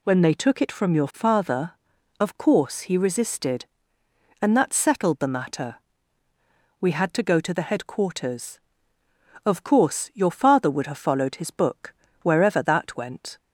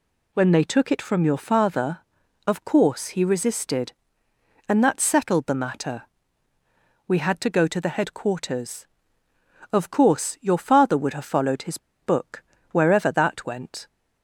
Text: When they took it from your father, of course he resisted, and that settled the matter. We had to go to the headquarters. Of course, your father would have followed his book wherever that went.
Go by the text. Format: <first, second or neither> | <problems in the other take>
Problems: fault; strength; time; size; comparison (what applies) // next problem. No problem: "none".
first | pauses between "his" and "book"; slight; at 11.7 s; 0.23 s long // pauses between "book" and "wherever"; slight; at 12.4 s; 0.28 s long; slight in the first